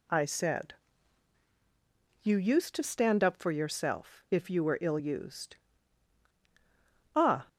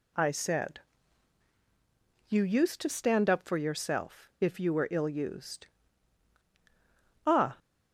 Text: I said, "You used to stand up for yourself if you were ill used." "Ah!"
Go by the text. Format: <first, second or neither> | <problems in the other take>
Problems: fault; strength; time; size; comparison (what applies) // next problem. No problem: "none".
neither | none